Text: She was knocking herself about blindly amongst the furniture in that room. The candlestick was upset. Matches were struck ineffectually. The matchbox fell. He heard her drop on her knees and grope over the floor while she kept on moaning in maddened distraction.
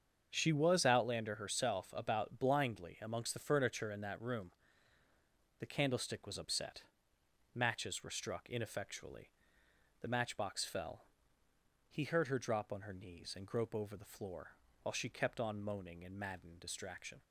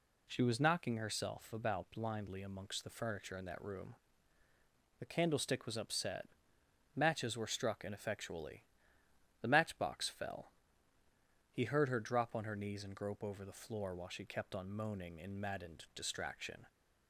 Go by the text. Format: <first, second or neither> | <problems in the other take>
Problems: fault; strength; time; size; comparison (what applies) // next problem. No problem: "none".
second | starts louder than the rest; until 1.3 s; 7 dB // says "outlander" for "knocking"; at 0.8 s // pauses between "floor" and "while"; slight; at 14.5 s; 0.28 s long